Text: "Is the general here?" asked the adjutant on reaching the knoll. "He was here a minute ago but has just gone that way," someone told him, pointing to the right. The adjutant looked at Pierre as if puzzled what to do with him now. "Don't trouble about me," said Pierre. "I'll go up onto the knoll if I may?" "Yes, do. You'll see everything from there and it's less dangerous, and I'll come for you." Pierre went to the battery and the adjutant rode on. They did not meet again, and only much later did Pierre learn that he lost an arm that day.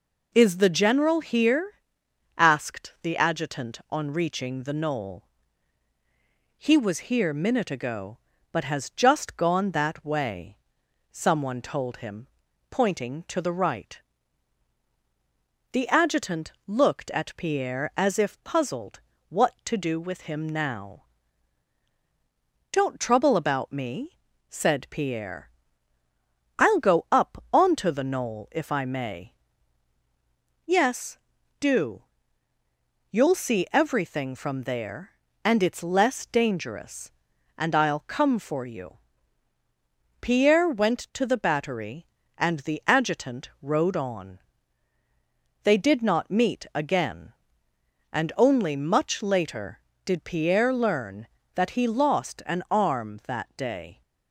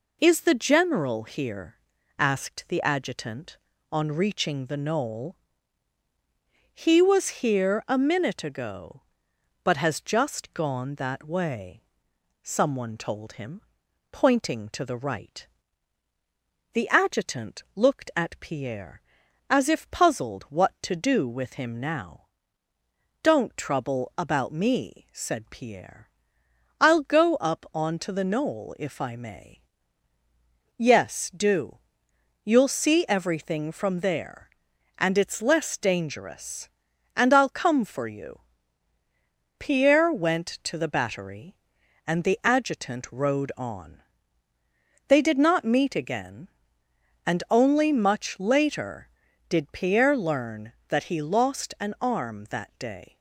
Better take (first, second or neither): second